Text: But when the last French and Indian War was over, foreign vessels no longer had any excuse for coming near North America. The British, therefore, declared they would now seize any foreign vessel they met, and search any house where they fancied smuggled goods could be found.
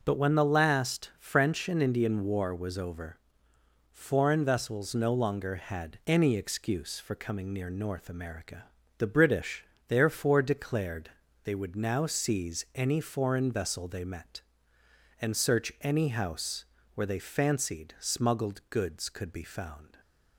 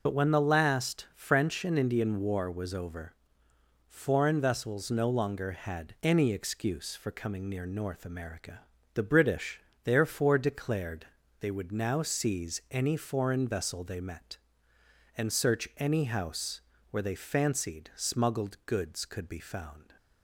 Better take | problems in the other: first | loses the start of "But"; at 0.0 s; 80 ms // pauses between "declared" and "they"; slight; at 11.0 s; 0.34 s long; slight in the first // pauses between "house" and "where"; slight; at 16.5 s; 0.32 s long; slight in the first

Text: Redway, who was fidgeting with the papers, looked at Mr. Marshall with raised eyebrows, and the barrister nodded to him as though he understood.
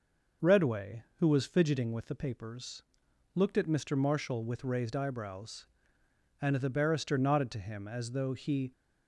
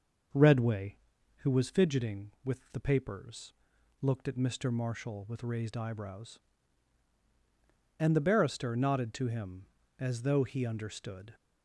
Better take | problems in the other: second | stops before "understood"; at 8.7 s

